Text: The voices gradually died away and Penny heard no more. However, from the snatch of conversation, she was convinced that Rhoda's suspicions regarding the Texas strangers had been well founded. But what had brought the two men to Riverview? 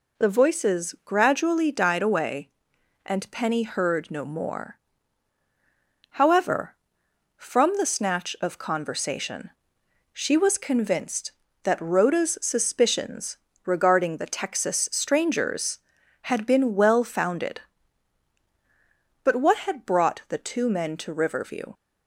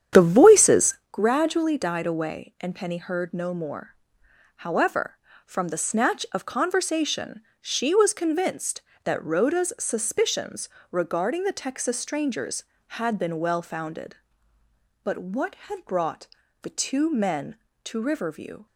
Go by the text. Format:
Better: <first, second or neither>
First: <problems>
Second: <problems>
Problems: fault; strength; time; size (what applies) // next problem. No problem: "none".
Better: first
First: pauses between "suspicions" and "regarding"; slight; at 13.3 s; 0.28 s long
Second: starts louder than the rest; strong; until 1.1 s; 9 dB // pauses between "voices" and "gradually"; slight; at 0.9 s; 0.16 s long // pauses between "suspicions" and "regarding"; slight; at 10.6 s; 0.24 s long // pauses between "brought" and "the"; slight; at 16.2 s; 0.34 s long